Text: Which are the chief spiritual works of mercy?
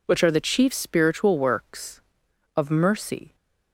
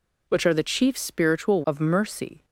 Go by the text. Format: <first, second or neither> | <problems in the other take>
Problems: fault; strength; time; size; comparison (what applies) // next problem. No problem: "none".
first | skips "works"; at 1.6 s